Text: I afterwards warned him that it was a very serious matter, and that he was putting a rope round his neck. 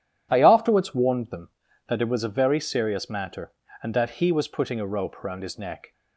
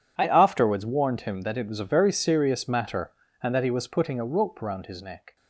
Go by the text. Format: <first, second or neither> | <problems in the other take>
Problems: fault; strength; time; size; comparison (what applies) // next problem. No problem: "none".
second | says "them" for "him"; at 1.3 s